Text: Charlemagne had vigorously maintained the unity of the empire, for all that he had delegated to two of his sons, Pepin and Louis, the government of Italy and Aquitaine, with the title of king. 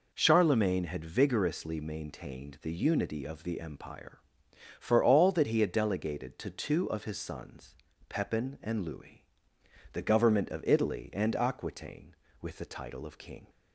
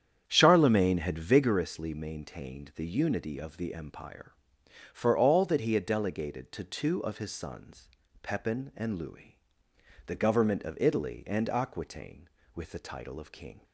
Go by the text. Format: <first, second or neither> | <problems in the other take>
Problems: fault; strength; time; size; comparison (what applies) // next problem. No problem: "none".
first | starts louder than the rest; strong; until 1.7 s; 8.5 dB